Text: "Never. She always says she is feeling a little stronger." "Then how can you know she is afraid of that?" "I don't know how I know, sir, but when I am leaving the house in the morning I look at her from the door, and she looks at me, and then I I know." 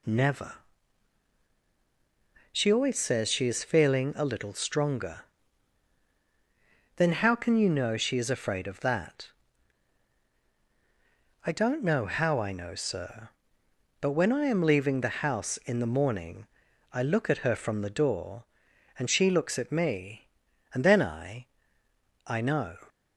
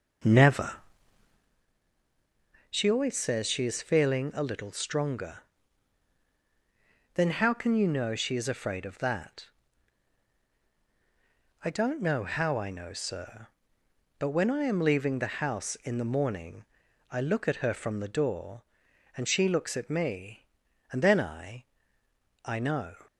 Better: first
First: pauses between "morning" and "I"; at 16.4 s; 0.44 s long // pauses between "I" and "I"; noticeable; at 21.4 s; 0.78 s long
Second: starts louder than the rest; noticeable; until 1.6 s; 6 dB // pauses between "morning" and "I"; at 16.6 s; 0.44 s long // pauses between "I" and "I"; noticeable; at 21.6 s; 0.78 s long

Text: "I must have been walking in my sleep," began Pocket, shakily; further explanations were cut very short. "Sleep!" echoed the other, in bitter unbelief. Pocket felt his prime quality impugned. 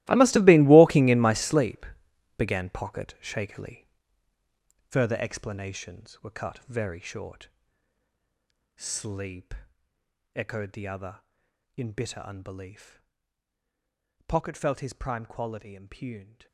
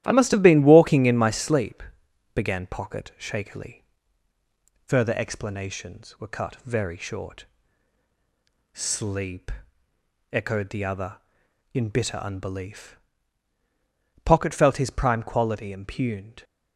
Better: second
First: gets quieter; strong; throughout; 17 dB // starts louder than the rest; strong; until 1.0 s; 17 dB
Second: starts louder than the rest; strong; until 1.0 s; 12.5 dB

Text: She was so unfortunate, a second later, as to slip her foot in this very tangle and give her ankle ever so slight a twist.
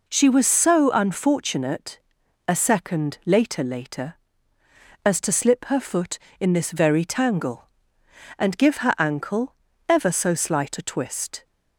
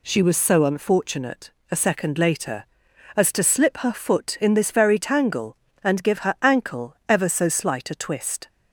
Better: second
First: says "later" twice; at 3.6 s // pauses between "ankle" and "ever"; slight; at 9.5 s; 0.34 s long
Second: none

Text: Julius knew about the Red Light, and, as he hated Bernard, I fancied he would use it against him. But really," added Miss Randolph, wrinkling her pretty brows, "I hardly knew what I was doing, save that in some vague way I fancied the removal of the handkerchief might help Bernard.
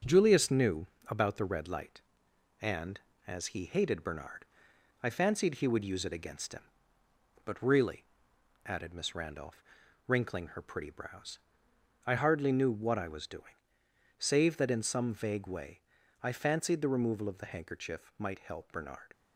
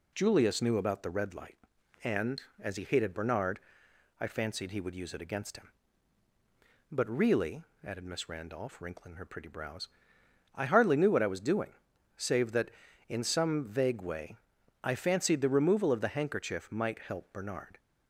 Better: second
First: gets quieter; noticeable; throughout; 5 dB // pauses between "knew" and "about"; slight; at 0.8 s; 0.22 s long // pauses between "way" and "I"; at 15.7 s; 0.42 s long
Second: pauses between "way" and "I"; noticeable; at 14.3 s; 0.46 s long

